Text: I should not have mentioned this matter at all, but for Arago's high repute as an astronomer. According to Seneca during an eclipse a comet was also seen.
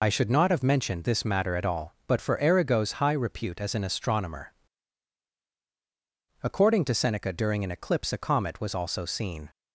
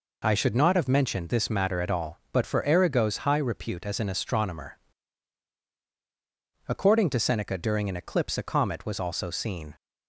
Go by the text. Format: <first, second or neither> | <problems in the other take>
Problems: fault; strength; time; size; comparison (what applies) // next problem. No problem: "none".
second | loses the start of "I"; at 0.0 s; 45 ms